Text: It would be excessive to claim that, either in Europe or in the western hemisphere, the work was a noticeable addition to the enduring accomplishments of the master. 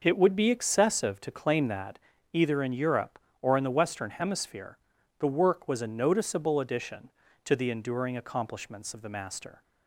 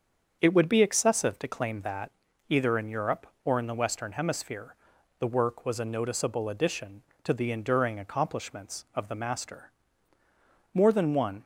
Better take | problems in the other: first | starts louder than the rest; until 1.4 s; 7 dB // goes on to say "More than one"; noticeable; from 10.7 s on; 0.70 s long

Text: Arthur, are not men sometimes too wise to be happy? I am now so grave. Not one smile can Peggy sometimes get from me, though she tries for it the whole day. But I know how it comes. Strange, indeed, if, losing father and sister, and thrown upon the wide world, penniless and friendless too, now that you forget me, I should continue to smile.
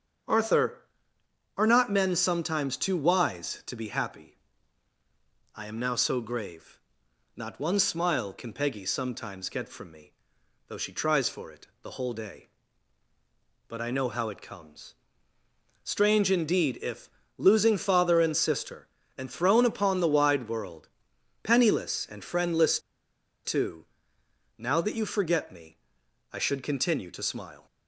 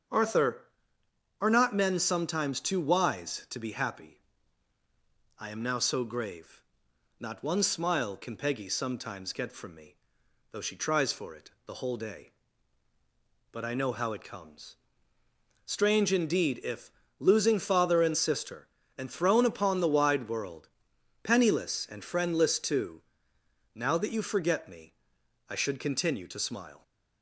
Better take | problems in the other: second | starts louder than the rest; strong; until 2.0 s; 7.5 dB; strong in the second // pauses between "it" and "the"; slight; at 11.6 s; 0.16 s long; slight in the second // pauses between "friendless" and "too"; noticeable; at 22.7 s; 0.66 s long

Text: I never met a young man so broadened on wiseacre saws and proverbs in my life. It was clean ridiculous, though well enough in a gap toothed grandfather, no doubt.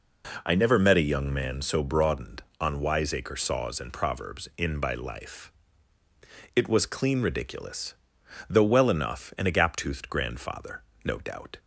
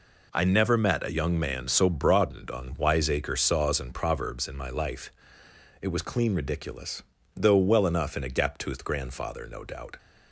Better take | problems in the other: second | says "by" for "my"; at 4.7 s

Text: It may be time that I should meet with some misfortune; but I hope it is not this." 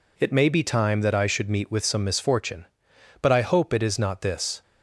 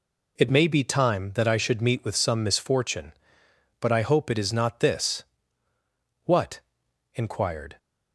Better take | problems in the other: first | goes on to say "What inquired"; from 6.2 s on; 1.5 s long

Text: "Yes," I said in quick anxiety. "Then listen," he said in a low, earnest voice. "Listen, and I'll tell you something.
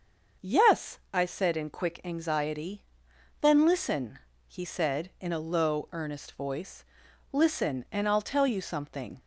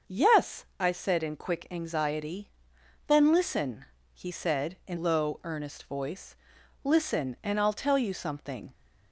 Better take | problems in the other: first | starts louder than the rest; until 1.1 s; 6.5 dB; also in the first // skips "a"; at 4.9 s

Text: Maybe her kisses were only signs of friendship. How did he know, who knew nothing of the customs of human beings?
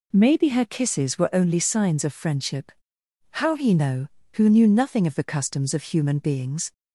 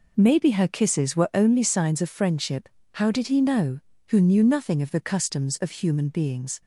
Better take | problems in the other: second | skips "did"; at 3.5 s

